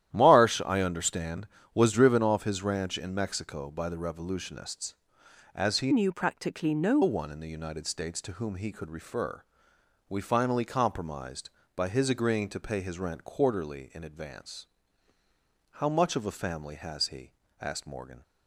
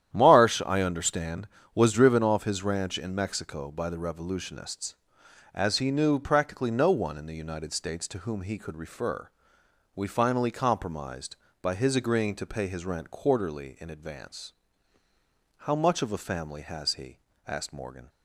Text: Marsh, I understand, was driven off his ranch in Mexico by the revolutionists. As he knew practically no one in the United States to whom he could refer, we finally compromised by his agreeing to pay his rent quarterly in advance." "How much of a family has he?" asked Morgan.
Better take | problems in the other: second | starts louder than the rest; strong; until 1.1 s; 12 dB; strong in the second // changes voice from "knew" to "no"; from 5.9 to 6.9 s; 1.0 s long

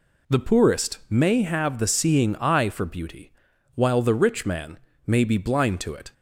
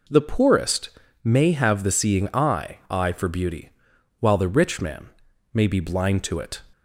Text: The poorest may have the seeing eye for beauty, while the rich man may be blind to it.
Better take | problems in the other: first | pauses between "poorest" and "may"; slight; at 0.8 s; 0.36 s long // says "eye" twice; at 2.8 s // pauses between "man" and "may"; at 5.0 s; 0.44 s long; slight in the first

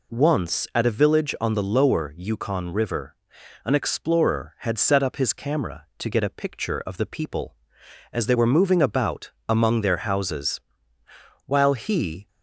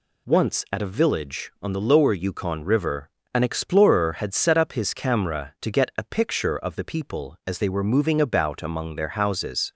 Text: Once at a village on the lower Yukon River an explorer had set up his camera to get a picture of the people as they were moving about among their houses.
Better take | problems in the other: second | pauses between "River" and "an"; noticeable; at 3.1 s; 0.48 s long; slight in the second // pauses between "about" and "among"; slight; at 9.3 s; 0.18 s long // goes on to say "While he"; noticeable; from 11.4 s on; 0.82 s long

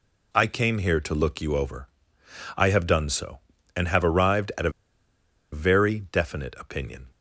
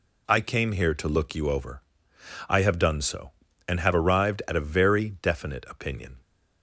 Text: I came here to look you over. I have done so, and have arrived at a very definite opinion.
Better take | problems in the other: second | pauses between "a" and "very"; noticeable; at 4.6 s; 0.82 s long

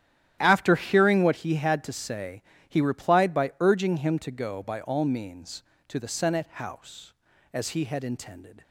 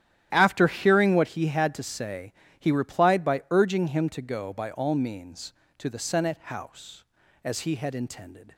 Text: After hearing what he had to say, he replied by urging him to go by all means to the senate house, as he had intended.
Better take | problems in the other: neither | starts louder than the rest; strong; the same in both

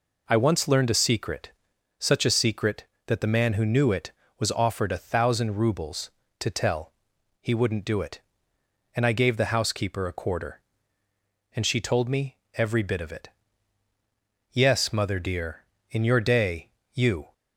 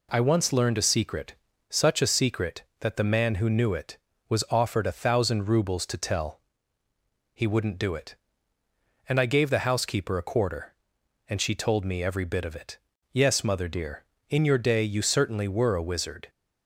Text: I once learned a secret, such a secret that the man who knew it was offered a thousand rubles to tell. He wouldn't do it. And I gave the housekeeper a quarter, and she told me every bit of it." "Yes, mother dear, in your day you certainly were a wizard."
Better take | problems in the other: second | pauses between "me" and "every"; slight; at 12.3 s; 0.18 s long // pauses between "day" and "you"; slight; at 16.6 s; 0.24 s long // stops before "certainly were a wizard"; at 17.3 s

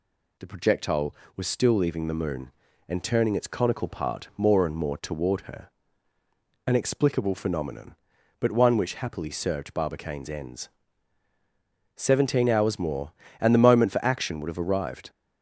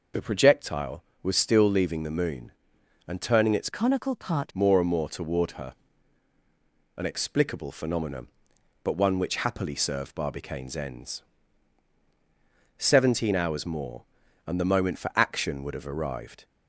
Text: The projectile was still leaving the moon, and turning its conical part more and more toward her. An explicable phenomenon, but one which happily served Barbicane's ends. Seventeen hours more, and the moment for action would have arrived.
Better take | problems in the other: first | changes voice from "conical" to "part"; from 3.6 to 4.5 s; 0.9 s long

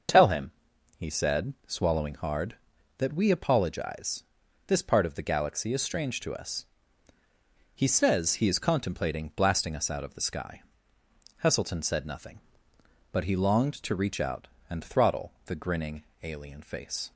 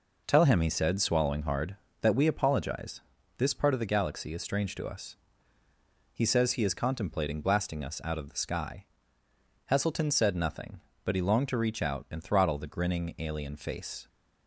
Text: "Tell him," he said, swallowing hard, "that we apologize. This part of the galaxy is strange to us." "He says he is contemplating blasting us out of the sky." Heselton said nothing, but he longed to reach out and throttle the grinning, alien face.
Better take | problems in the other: neither | none

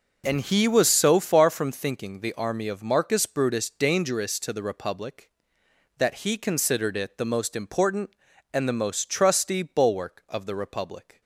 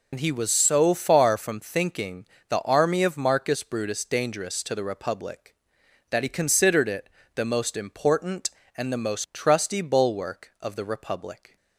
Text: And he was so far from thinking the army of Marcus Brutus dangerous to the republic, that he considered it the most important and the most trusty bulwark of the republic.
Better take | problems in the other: first | loses the start of "And"; at 0.1 s; 70 ms // pauses between "thinking" and "the"; slight; at 2.2 s; 0.22 s long // pauses between "it" and "the"; slight; at 7.0 s; 0.26 s long

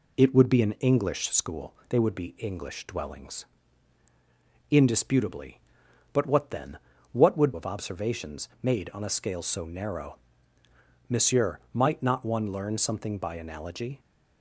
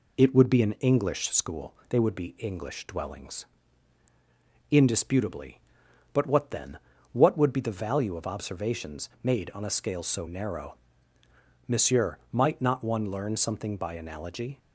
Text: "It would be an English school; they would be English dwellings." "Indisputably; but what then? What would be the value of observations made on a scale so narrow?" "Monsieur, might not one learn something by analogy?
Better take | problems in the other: second | skips "be the value"; at 7.5 s // pauses between "observations" and "made"; slight; at 8.4 s; 0.16 s long; slight in the second

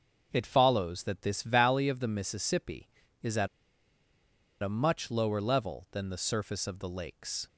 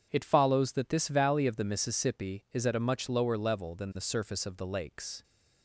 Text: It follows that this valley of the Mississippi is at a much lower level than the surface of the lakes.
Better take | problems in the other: second | starts louder than the rest; noticeable; until 1.3 s; 6 dB; strong in the second // pauses between "at" and "a"; at 3.4 s; 1.1 s long

